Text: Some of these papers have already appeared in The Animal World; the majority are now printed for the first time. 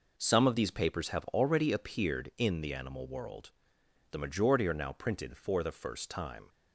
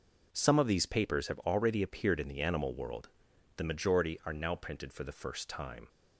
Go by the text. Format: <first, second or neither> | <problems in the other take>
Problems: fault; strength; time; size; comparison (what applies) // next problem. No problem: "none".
neither | none